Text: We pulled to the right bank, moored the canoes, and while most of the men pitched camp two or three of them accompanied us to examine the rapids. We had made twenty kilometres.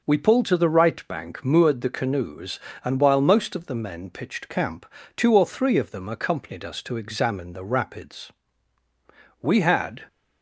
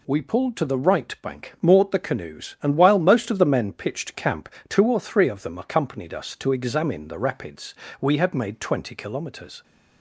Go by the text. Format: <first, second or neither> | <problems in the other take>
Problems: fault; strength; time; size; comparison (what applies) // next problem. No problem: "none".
second | pauses between "camp" and "two"; slight; at 4.8 s; 0.32 s long; slight in the second // stops before "made twenty kilometres"; at 10.0 s